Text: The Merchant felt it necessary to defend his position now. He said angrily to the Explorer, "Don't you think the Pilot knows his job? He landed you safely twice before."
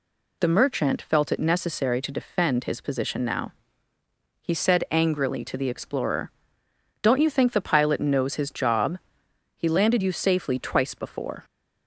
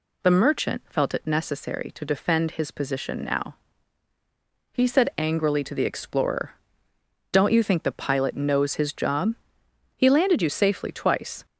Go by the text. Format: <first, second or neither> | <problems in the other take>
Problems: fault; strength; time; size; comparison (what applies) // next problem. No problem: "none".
first | stops before "before"; at 11.4 s